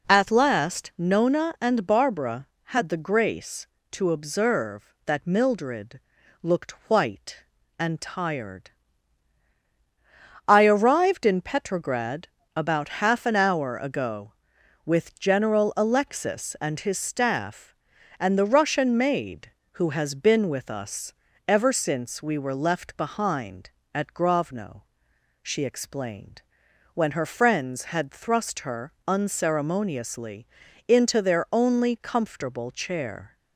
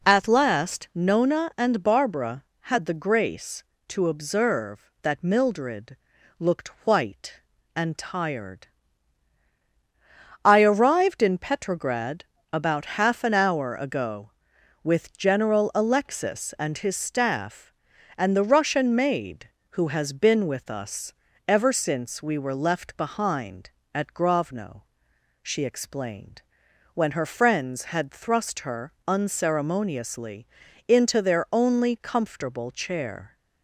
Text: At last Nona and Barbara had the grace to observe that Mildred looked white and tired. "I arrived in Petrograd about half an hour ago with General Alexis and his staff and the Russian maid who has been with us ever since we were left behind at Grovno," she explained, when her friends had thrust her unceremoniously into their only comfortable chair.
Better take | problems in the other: neither | pauses between "Mildred" and "looked"; the same in both // pauses between "looked" and "white"; slight; the same in both // pauses between "Petrograd" and "about"; slight; the same in both // pauses between "us" and "ever"; slight; the same in both // pauses between "her" and "unceremoniously"; slight; the same in both // pauses between "unceremoniously" and "into"; the same in both

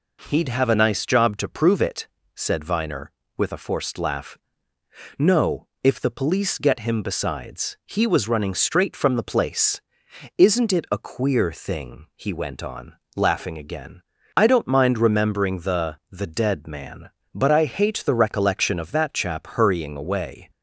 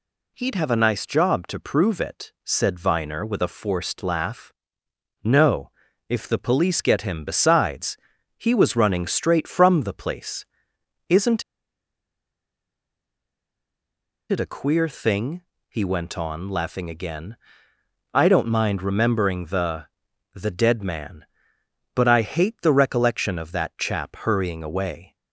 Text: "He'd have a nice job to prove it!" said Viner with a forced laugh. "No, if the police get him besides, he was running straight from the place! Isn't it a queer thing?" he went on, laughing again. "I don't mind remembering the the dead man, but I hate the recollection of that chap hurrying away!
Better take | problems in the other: first | pauses between "Isn't" and "it"; strong; at 11.4 s; 2.8 s long // pauses between "the" and "the"; noticeable; at 19.8 s; 0.48 s long

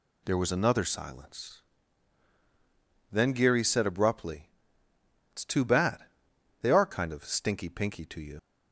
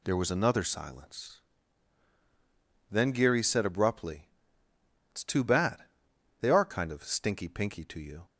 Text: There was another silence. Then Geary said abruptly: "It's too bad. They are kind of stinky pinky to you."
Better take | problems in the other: second | leaves "you" unfinished; at 8.3 s; 65 ms

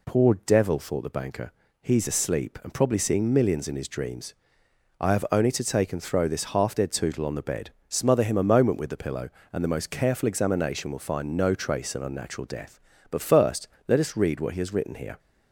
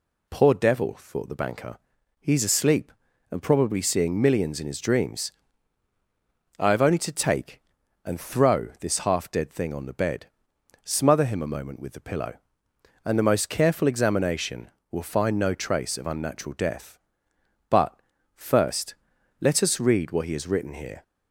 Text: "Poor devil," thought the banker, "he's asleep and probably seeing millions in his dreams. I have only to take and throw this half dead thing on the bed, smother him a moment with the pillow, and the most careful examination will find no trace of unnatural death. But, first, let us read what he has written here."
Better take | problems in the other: second | says "tootle" for "thing"; at 6.9 s

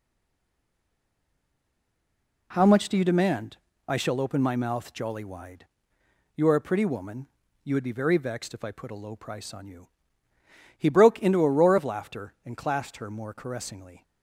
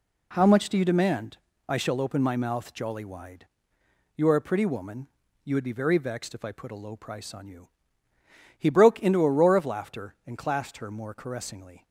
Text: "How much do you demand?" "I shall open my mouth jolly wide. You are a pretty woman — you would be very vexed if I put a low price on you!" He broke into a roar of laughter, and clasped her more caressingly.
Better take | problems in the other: second | stays silent before the first word; until 2.5 s; 2.5 s long

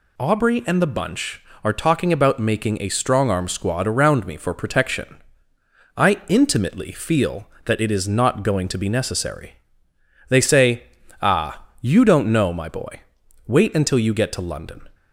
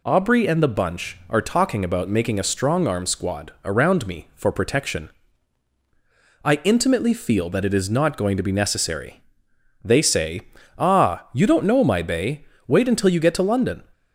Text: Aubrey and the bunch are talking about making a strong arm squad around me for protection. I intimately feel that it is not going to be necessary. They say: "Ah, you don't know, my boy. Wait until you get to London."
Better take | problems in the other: first | says "bay" for "boy"; at 12.0 s

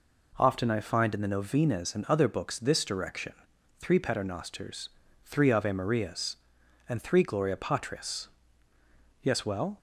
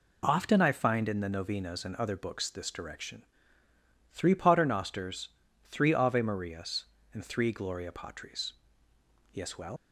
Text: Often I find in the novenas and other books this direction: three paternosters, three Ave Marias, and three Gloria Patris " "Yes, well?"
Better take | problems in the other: first | leaves "well" unfinished; at 9.7 s; 95 ms

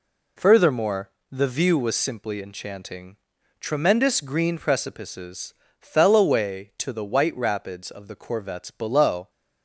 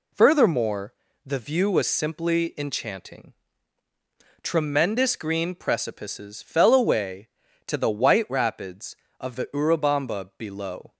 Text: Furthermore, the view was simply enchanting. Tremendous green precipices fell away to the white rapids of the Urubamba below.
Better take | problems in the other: second | pauses between "precipices" and "fell"; slight; at 5.5 s; 0.30 s long // says "Corvettes" for "Urubamba"; at 8.1 s

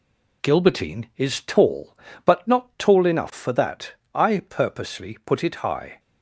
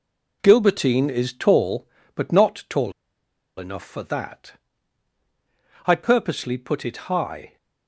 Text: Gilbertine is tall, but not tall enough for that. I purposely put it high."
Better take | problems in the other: first | pauses between "tall" and "enough"; noticeable; at 2.9 s; 0.66 s long // pauses between "it" and "high"; slight; at 6.9 s; 0.16 s long

